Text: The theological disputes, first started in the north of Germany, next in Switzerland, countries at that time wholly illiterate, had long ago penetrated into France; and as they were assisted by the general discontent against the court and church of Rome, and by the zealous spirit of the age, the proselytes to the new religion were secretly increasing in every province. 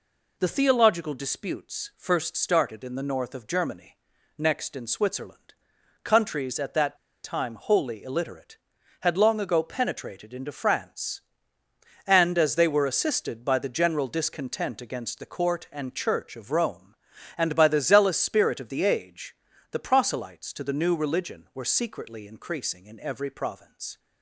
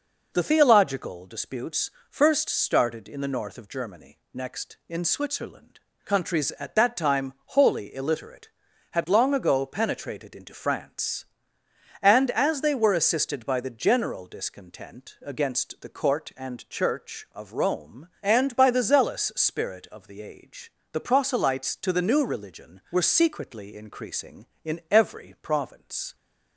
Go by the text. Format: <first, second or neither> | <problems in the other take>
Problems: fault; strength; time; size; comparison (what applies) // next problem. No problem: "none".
second | pauses between "that" and "time"; slight; at 6.9 s; 0.27 s long